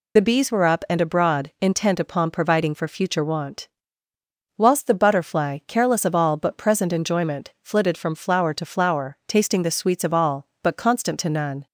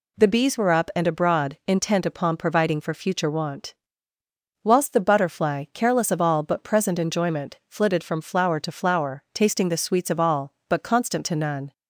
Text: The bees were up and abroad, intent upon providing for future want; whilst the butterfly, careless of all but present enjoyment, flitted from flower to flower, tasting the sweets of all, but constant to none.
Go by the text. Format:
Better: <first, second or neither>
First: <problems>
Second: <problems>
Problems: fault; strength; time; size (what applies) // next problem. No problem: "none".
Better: second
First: loses the start of "The"; at 0.1 s; 55 ms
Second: none